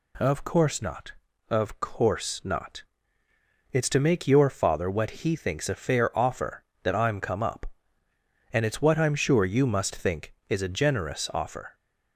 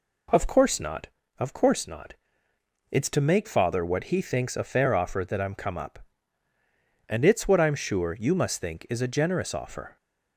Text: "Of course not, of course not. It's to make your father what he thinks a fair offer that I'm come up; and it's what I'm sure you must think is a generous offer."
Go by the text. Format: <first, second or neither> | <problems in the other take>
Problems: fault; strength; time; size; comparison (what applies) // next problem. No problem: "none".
first | skips "your"; at 3.4 s